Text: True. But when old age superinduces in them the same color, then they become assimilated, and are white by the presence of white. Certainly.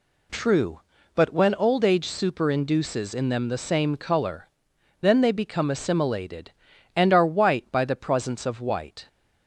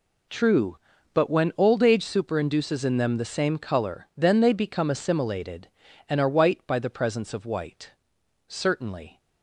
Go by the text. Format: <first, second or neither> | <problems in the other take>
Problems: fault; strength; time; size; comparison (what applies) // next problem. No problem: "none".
second | stops before "Certainly"; at 9.0 s